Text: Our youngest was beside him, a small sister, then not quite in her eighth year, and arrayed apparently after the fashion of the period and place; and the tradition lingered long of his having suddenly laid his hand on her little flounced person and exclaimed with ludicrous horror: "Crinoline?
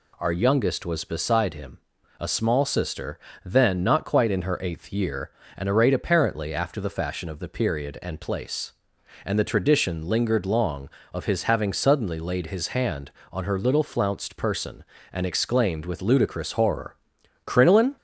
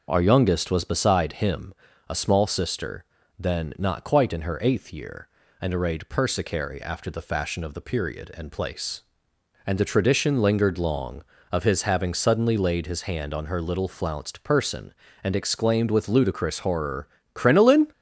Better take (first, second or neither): first